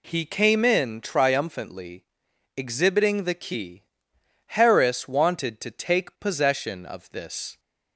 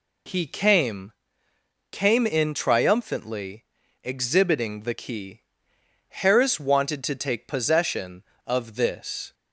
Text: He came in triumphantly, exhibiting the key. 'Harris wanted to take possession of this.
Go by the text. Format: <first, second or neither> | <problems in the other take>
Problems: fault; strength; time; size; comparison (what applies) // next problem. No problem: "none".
first | says "came" twice; at 1.9 s